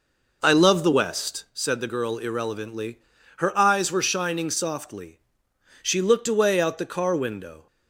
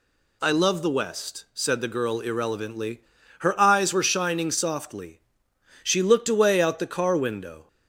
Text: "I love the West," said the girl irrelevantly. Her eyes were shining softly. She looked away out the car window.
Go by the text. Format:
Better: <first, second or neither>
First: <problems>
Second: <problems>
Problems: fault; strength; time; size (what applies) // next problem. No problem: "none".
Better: second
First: starts louder than the rest; noticeable; until 1.5 s; 5 dB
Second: none